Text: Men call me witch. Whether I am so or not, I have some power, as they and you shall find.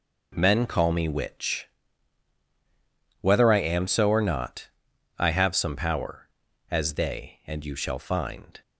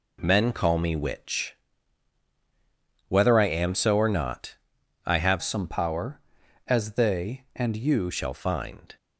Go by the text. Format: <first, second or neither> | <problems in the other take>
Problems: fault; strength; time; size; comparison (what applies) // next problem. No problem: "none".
first | changes voice from "some" to "you"; from 5.4 to 8.1 s; 2.7 s long